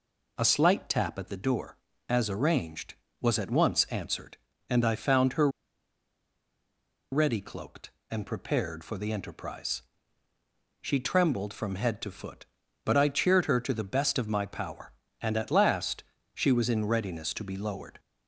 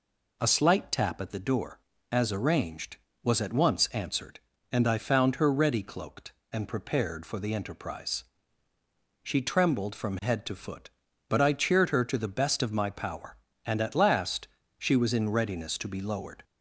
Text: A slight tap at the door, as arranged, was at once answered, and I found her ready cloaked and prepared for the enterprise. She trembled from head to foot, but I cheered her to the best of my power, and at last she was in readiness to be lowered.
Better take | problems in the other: second | pauses between "her" and "ready"; strong; at 5.4 s; 1.6 s long // pauses between "last" and "she"; slight; at 16.0 s; 0.30 s long; slight in the second

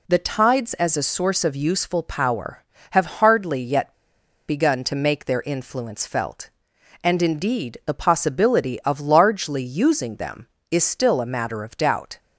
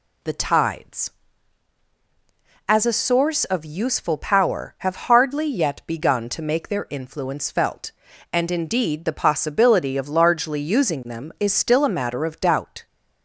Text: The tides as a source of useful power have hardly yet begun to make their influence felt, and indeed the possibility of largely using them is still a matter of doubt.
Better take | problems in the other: second | pauses between "yet" and "begun"; noticeable; at 3.9 s; 0.55 s long

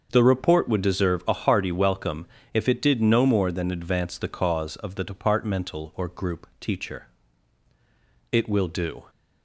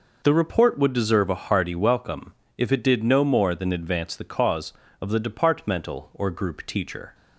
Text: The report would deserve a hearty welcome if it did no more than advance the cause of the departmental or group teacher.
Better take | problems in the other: second | starts louder than the rest; until 1.1 s; 6.5 dB // pauses between "welcome" and "if"; slight; at 2.2 s; 0.26 s long; slight in the second // goes on to say "It will do"; noticeable; from 8.3 s on; 0.72 s long

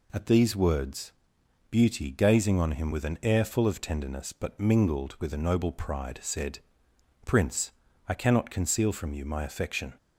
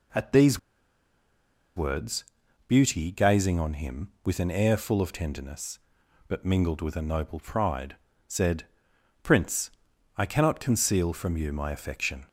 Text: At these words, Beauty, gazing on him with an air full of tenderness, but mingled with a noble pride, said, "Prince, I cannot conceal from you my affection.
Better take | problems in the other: first | pauses between "these" and "words"; at 0.5 s; 1.1 s long

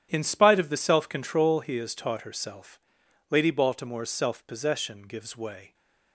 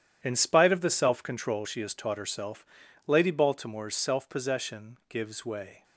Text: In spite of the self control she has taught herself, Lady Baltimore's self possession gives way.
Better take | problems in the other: second | starts louder than the rest; strong; until 1.1 s; 9.5 dB; strong in the second // says "he" for "she"; at 1.5 s

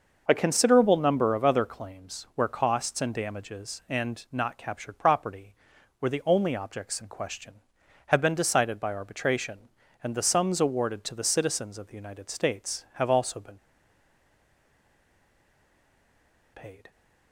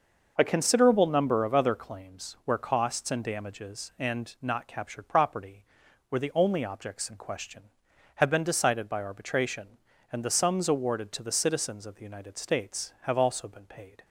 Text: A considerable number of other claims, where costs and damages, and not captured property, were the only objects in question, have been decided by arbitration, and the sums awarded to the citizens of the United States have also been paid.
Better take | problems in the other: second | pauses between "been" and "paid"; strong; at 13.5 s; 2.9 s long

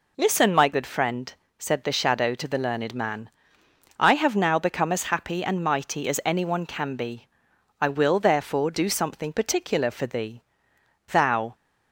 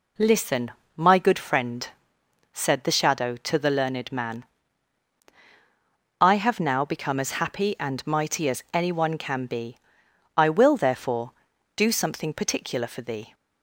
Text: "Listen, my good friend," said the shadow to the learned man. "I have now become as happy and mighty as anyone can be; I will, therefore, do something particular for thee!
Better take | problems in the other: second | goes on to say "Thou"; slight; from 11.0 s on; 0.46 s long

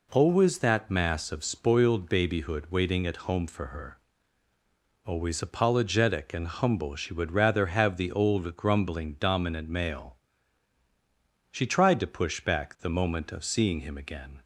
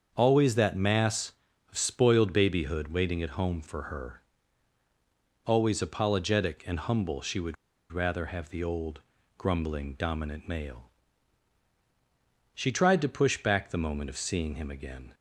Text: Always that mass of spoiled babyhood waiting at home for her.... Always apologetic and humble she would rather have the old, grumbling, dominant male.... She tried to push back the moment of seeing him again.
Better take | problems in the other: first | starts louder than the rest; until 1.1 s; 7 dB // pauses between "would" and "rather"; at 7.5 s; 0.37 s long

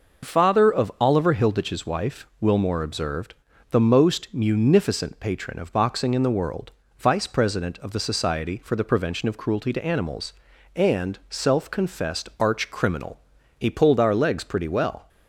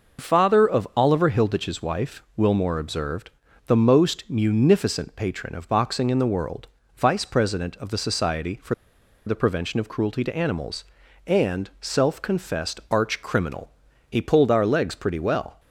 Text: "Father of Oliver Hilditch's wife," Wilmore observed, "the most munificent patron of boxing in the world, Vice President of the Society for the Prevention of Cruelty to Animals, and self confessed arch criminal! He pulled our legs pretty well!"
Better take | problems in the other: first | pauses between "for" and "the"; noticeable; at 8.7 s; 0.53 s long

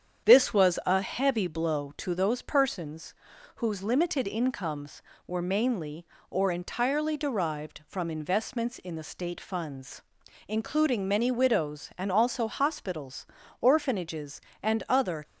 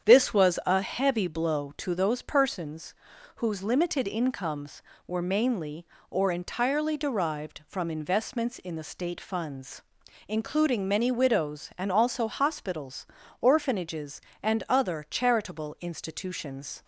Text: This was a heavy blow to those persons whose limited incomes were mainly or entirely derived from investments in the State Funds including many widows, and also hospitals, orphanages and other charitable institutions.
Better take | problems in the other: second | starts louder than the rest; strong; until 1.3 s; 8 dB; strong in the second // pauses between "persons" and "whose"; at 3.1 s; 0.42 s long; also in the second // pauses between "Funds" and "including"; noticeable; at 10.0 s; 0.46 s long; noticeable in the second // stops before "charitable institutions"; at 15.2 s

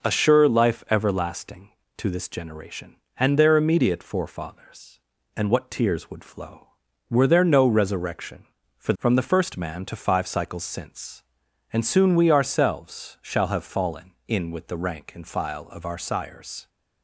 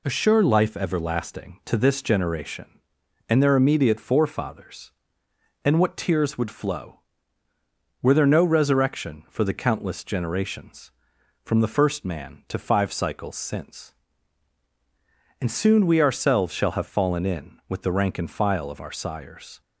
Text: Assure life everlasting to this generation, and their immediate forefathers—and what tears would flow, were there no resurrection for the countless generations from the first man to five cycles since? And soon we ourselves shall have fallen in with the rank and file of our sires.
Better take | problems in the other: second | skips "the countless generations"; at 8.9 s

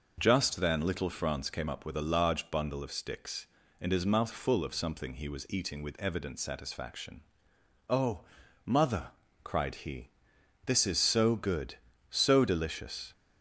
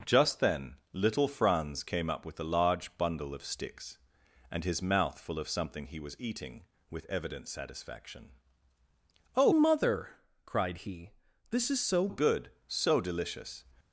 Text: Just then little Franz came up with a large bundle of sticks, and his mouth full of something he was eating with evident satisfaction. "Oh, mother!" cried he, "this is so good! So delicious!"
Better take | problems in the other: first | pauses between "then" and "little"; slight; at 0.7 s; 0.18 s long // changes voice from "mother" to "so"; from 9.5 to 12.0 s; 2.5 s long

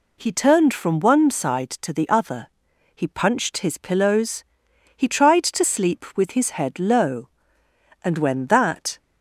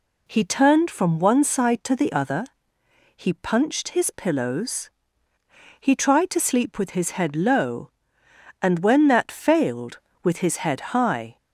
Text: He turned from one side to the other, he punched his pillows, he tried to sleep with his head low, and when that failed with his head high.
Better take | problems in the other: second | stops before "failed with his head high"; at 8.9 s

